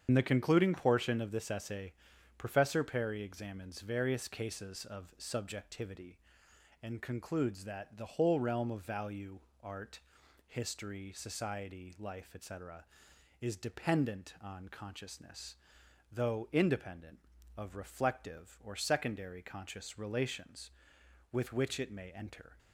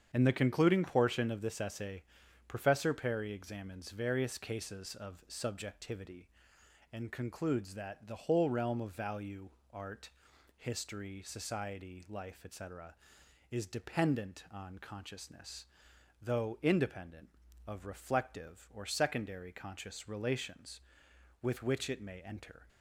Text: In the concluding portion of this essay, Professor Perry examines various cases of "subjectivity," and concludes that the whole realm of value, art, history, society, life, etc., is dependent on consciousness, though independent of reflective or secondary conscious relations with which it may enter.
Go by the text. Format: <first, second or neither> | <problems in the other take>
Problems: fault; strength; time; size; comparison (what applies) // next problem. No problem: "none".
second | loses the start of "In"; at 0.0 s; 50 ms // starts louder than the rest; strong; until 1.0 s; 8 dB; strong in the second